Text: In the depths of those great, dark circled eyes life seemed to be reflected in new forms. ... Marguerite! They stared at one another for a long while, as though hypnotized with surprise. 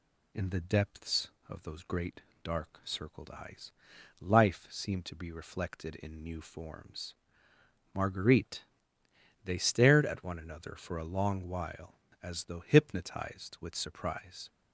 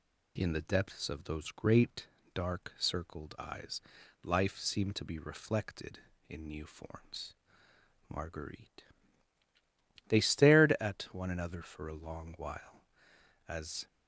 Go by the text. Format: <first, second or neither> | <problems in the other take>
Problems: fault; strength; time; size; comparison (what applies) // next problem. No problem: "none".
first | pauses between "eyes" and "life"; at 3.8 s; 0.42 s long; noticeable in the first // stops before "though hypnotized with surprise"; at 13.8 s